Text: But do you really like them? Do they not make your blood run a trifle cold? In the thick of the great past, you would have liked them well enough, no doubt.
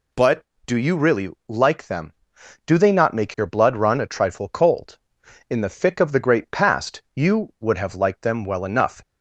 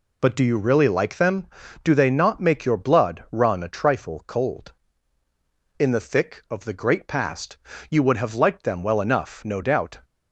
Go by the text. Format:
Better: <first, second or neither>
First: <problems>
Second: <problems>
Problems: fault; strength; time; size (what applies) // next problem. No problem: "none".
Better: second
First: pauses between "really" and "like"; slight; at 1.3 s; 0.18 s long // stops before "no doubt"; at 9.0 s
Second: none